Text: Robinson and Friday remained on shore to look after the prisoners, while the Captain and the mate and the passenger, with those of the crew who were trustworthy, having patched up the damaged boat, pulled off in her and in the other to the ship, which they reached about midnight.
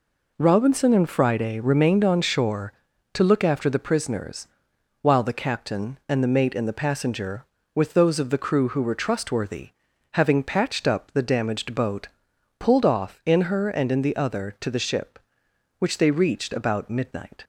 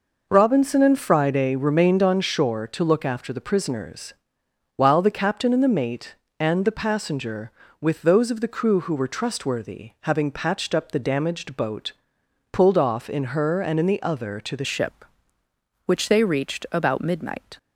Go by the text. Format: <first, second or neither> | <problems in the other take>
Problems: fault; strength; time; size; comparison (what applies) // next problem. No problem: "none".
first | changes voice at "ship"; from 14.6 s on; 2.9 s long